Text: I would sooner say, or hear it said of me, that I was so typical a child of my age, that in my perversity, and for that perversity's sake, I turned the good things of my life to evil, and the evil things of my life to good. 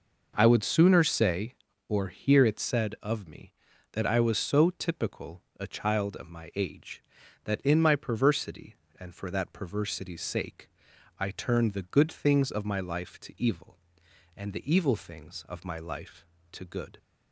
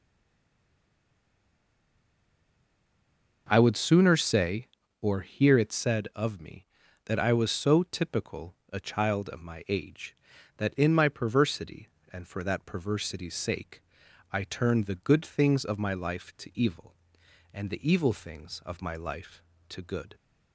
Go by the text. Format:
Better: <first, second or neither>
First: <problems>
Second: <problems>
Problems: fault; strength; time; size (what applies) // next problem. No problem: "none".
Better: first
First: pauses between "typical" and "a"; slight; at 5.4 s; 0.18 s long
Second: stays silent before the first word; strong; until 3.4 s; 3.4 s long // pauses between "typical" and "a"; slight; at 8.5 s; 0.18 s long